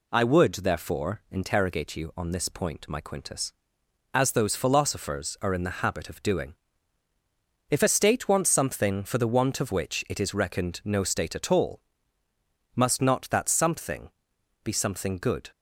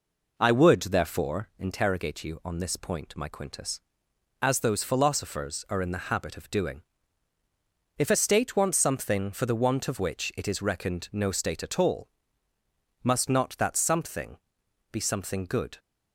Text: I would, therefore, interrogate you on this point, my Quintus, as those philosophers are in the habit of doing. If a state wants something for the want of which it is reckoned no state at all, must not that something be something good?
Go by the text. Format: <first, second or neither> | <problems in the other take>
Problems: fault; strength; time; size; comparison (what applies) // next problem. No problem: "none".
first | starts louder than the rest; noticeable; until 1.3 s; 4.5 dB // pauses between "something" and "be"; noticeable; at 14.3 s; 0.54 s long; noticeable in the first